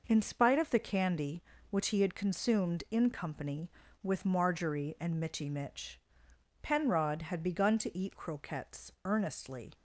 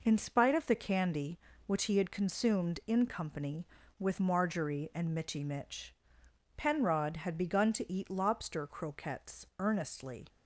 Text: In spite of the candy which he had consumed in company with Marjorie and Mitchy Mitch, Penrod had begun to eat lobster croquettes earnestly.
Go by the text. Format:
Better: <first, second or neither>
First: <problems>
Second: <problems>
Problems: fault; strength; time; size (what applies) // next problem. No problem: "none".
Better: second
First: skips "lobster"; at 8.1 s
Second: none